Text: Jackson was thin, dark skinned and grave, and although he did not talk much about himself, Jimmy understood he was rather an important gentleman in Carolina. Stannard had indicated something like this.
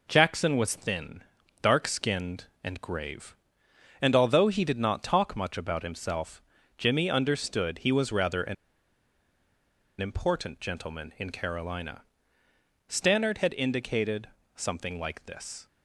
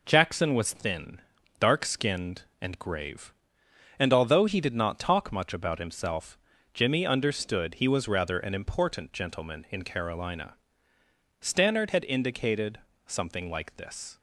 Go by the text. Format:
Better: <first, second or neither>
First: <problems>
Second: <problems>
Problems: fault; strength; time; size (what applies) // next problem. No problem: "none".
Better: second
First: pauses between "an" and "important"; strong; at 8.5 s; 1.4 s long // pauses between "indicated" and "something"; slight; at 14.2 s; 0.26 s long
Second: pauses between "indicated" and "something"; slight; at 12.7 s; 0.26 s long